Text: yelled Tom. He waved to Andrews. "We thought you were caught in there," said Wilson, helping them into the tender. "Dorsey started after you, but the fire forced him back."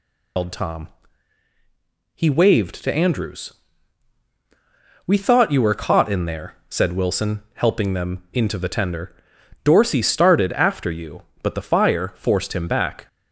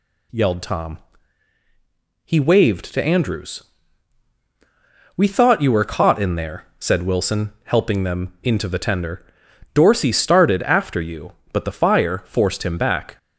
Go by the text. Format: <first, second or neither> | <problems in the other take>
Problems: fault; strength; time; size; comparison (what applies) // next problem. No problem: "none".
second | loses the start of "yelled"; at 0.3 s; 145 ms